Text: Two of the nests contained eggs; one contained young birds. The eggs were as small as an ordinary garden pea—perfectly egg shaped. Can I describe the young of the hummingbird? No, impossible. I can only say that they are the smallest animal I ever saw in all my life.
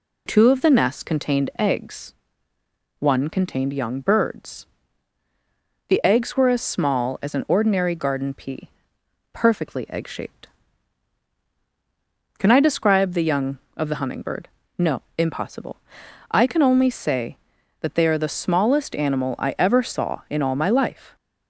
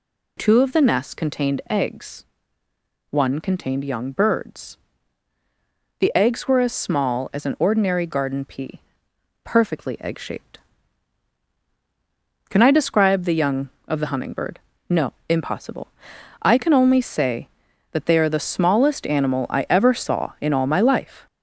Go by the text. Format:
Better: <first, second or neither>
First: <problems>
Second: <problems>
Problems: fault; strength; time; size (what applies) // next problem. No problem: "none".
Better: first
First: none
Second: gets louder; noticeable; throughout; 4 dB